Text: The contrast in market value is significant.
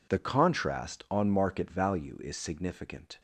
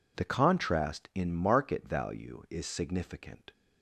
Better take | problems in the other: second | says "on" for "in"; at 1.0 s

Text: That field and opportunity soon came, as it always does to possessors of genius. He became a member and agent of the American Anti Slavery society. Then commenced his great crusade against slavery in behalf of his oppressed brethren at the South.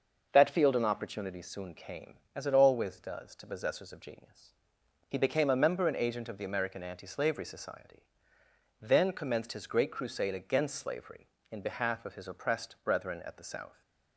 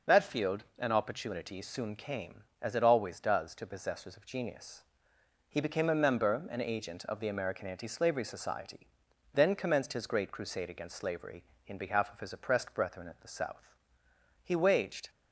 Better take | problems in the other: first | goes on to say "He waged"; noticeable; from 14.4 s on; 0.66 s long

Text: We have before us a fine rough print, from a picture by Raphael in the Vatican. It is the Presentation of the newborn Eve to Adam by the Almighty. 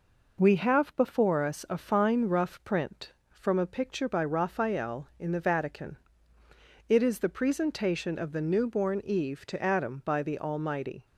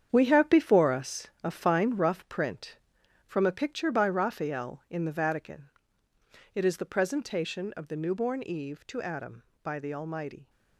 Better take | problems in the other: first | gets quieter; strong; throughout; 10 dB // pauses between "us" and "a"; slight; at 1.2 s; 0.16 s long

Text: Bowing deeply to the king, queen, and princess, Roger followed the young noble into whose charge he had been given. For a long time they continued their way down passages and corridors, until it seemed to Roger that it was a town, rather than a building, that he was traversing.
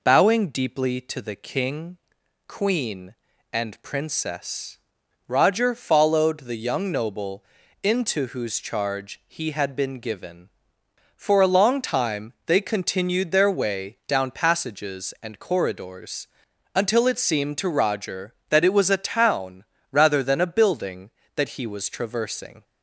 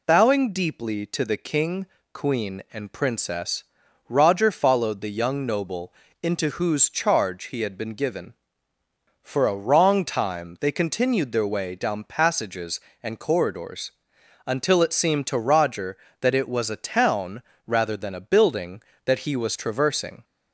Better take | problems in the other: first | pauses between "noble" and "into"; slight; at 5.9 s; 0.28 s long; also in the first // says "wrong" for "long"; at 9.5 s

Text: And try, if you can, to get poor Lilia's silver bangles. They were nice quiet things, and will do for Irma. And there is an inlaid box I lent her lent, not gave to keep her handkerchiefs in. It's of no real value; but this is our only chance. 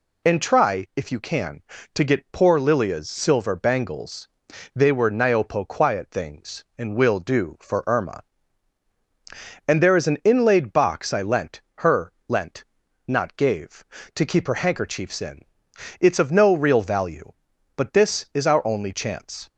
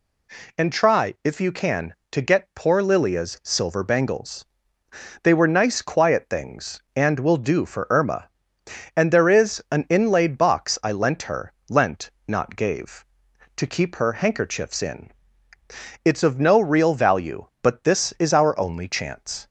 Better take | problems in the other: second | says "niopo" for "nice"; at 5.0 s // pauses between "her" and "lent"; slight; at 12.1 s; 0.16 s long; slight in the second

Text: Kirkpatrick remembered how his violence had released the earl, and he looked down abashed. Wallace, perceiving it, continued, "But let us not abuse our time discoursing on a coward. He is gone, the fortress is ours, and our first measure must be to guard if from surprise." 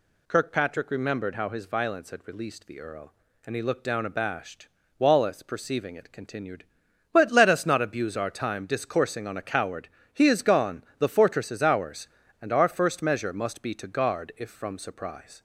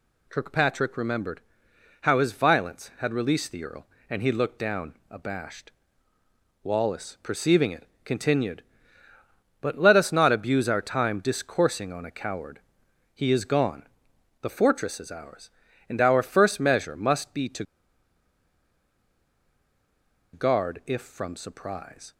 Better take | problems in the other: first | pauses between "remembered" and "how"; noticeable; at 1.4 s; 0.60 s long // pauses between "to" and "guard"; strong; at 17.6 s; 2.7 s long

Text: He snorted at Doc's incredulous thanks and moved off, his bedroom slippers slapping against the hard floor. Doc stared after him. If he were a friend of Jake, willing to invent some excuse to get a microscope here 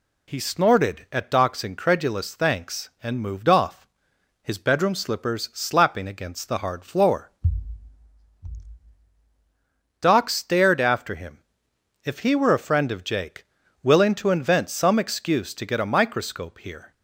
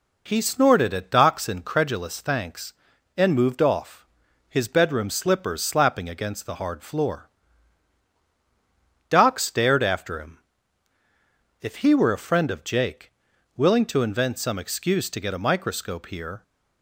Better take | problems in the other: neither | none

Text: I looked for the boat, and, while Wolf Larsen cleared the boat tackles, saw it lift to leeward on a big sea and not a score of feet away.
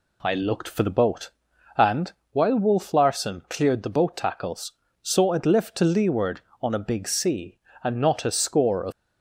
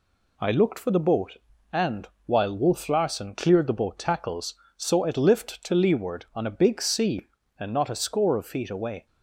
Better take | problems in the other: second | stops before "feet away"; at 8.9 s

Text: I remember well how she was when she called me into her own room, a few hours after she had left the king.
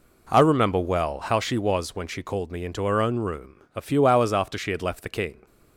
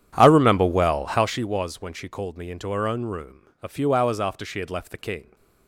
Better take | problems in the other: first | starts louder than the rest; strong; until 1.5 s; 9.5 dB

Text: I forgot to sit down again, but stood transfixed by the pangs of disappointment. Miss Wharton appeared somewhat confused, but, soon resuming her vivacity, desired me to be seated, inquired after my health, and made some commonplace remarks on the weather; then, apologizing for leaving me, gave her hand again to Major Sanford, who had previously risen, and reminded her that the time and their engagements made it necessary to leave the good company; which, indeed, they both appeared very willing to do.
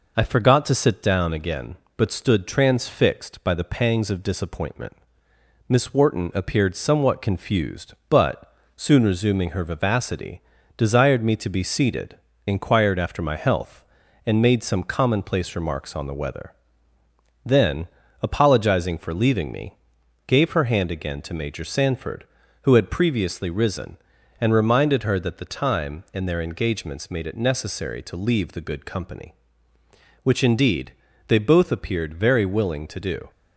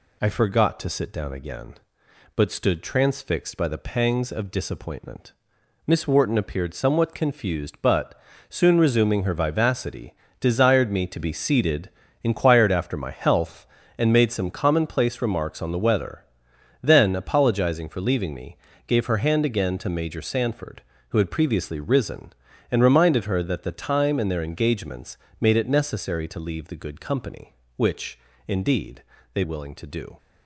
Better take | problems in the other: first | pauses between "engagements" and "made"; slight; at 25.1 s; 0.24 s long // skips "both appeared very"; at 29.4 s

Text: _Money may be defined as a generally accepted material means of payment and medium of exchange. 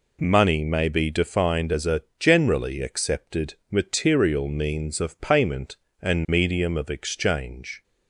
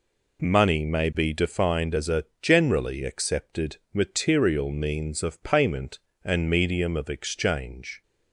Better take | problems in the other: neither | pauses between "a" and "generally"; slight; the same in both // pauses between "accepted" and "material"; slight; the same in both

